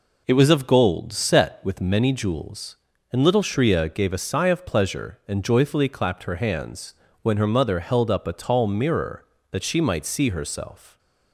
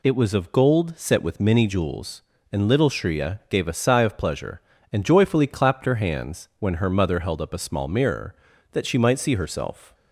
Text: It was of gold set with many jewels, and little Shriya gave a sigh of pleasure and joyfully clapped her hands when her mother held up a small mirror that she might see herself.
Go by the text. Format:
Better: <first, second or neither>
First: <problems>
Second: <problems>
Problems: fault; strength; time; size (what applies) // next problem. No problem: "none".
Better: second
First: pauses between "hands" and "when"; slight; at 6.9 s; 0.28 s long // says "tall" for "small"; at 8.3 s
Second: none